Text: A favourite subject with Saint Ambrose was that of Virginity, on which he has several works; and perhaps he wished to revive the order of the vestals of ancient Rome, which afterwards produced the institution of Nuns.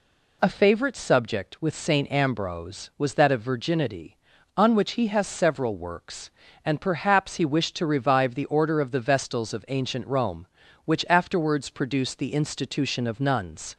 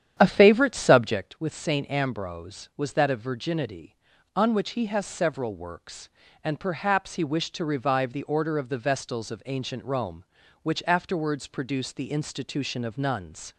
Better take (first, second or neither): first